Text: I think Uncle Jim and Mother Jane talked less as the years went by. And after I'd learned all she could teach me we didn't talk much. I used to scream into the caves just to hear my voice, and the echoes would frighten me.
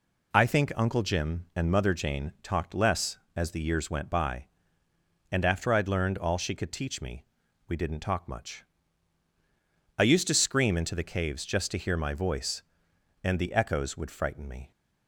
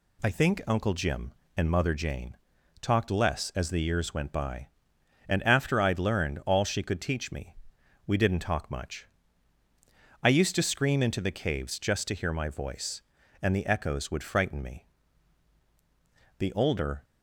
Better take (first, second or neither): first